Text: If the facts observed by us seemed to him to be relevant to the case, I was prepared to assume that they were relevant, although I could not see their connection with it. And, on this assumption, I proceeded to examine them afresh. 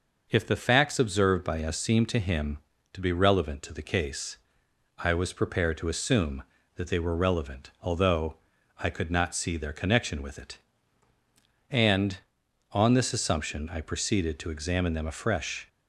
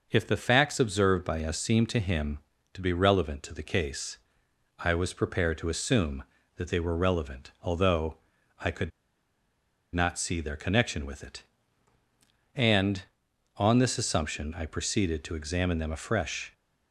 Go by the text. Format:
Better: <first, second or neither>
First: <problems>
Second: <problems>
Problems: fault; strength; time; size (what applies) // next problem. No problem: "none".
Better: first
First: pauses between "although" and "I"; at 8.3 s; 0.39 s long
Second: pauses between "although" and "I"; at 8.1 s; 0.40 s long // pauses between "could" and "not"; at 8.9 s; 1.0 s long